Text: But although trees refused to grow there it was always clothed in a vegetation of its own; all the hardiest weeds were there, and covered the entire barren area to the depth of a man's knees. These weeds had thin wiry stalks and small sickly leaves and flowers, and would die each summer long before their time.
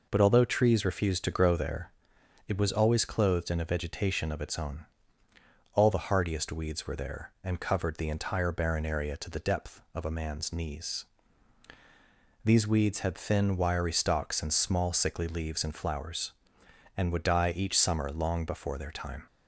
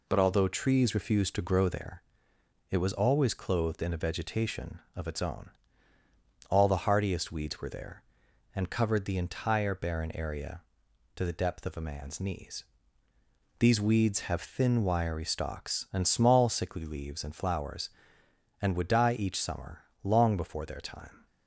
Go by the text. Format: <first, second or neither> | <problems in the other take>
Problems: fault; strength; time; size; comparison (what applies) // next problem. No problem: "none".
first | pauses between "there" and "it"; noticeable; at 2.0 s; 0.68 s long; noticeable in the first // says "have" for "had"; at 14.3 s // pauses between "summer" and "long"; slight; at 19.8 s; 0.20 s long